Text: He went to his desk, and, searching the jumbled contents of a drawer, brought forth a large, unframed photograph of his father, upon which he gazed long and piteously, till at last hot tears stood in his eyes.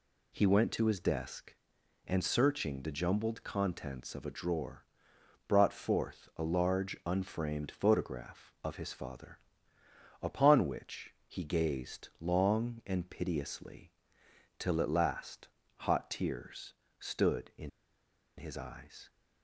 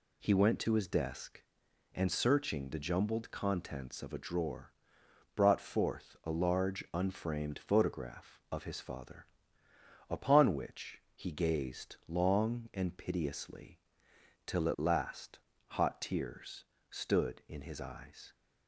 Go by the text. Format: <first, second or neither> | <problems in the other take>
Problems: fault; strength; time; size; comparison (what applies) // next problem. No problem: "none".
second | pauses between "last" and "hot"; slight; at 15.4 s; 0.28 s long; slight in the second // pauses between "tears" and "stood"; slight; at 16.7 s; 0.24 s long; slight in the second // pauses between "in" and "his"; noticeable; at 17.6 s; 0.67 s long